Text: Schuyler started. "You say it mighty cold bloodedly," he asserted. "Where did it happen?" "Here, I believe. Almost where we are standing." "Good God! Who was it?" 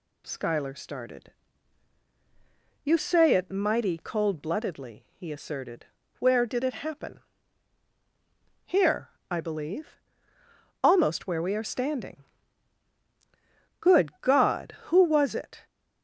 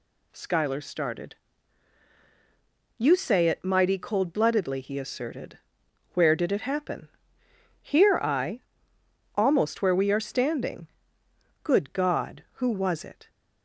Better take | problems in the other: first | skips "believe"; at 8.9 s

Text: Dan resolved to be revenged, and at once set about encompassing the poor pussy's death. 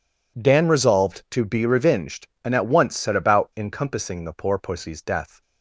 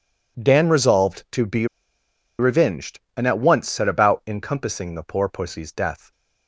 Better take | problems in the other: first | pauses between "be" and "revenged"; noticeable; at 1.6 s; 0.73 s long

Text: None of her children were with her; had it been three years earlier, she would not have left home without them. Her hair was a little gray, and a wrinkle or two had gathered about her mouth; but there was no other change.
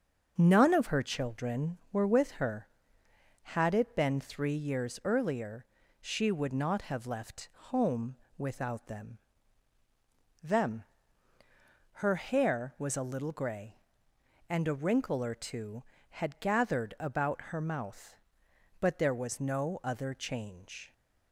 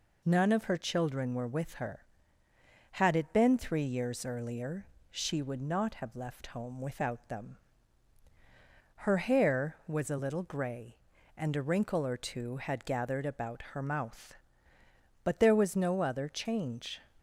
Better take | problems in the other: second | starts louder than the rest; noticeable; until 1.3 s; 6 dB // pauses between "left" and "home"; slight; at 7.4 s; 0.22 s long // pauses between "home" and "without"; slight; at 8.1 s; 0.20 s long // says "them" twice; at 10.4 s

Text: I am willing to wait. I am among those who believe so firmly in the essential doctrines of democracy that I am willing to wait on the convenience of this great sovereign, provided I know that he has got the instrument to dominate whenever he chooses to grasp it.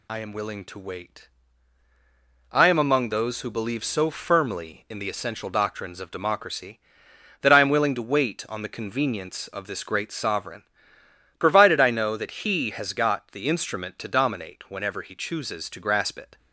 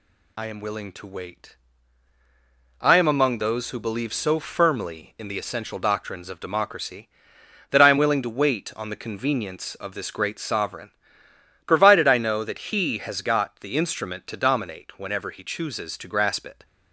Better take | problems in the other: neither | none

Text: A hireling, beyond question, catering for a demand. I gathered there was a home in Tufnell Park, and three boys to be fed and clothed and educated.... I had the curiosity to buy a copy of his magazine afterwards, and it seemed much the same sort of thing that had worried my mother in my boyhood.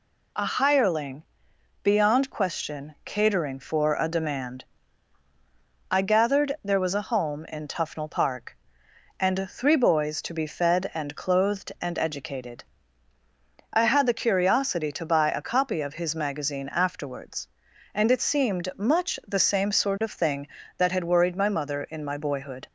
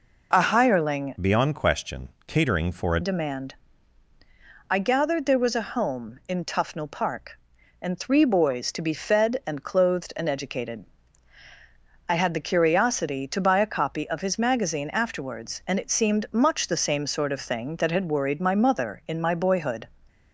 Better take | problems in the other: first | changes voice from "beyond" to "a"; from 1.2 to 2.9 s; 1.7 s long

